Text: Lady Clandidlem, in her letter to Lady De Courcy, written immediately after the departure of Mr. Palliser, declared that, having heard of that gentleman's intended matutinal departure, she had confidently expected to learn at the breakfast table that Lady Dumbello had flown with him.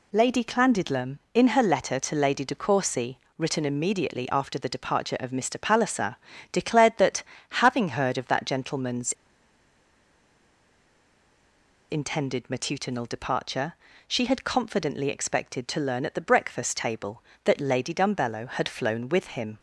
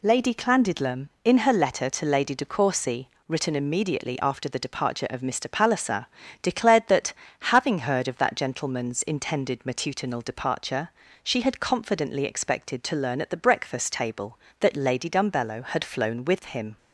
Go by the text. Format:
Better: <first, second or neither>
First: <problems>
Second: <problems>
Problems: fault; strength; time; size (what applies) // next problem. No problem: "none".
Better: second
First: pauses between "gentleman's" and "intended"; strong; at 9.1 s; 2.7 s long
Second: none